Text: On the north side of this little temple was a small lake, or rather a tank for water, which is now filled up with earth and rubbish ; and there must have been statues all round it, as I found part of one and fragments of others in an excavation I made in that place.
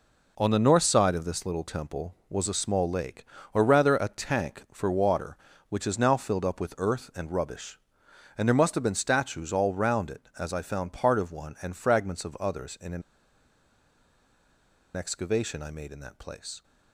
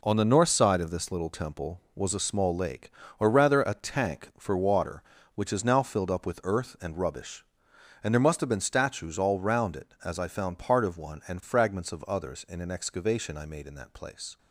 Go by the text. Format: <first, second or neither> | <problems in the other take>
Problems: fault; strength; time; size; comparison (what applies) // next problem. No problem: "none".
second | pauses between "an" and "excavation"; strong; at 13.0 s; 1.9 s long